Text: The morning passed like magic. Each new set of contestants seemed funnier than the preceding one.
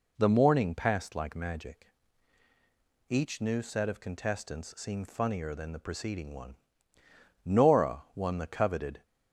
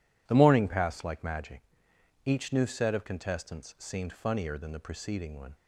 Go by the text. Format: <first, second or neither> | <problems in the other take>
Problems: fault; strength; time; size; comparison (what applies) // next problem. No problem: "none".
second | goes on to say "Nora won the coveted"; from 7.4 s on; 1.6 s long